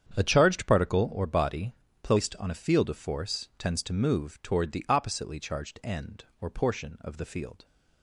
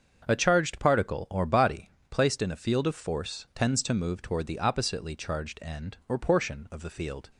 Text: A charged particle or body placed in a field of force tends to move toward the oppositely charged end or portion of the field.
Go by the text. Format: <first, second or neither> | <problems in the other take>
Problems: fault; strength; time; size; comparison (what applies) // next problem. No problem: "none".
second | starts louder than the rest; strong; until 1.2 s; 8.5 dB; also in the second // pauses between "body" and "placed"; slight; at 1.7 s; 0.28 s long; slight in the second // says "on" for "in"; at 2.3 s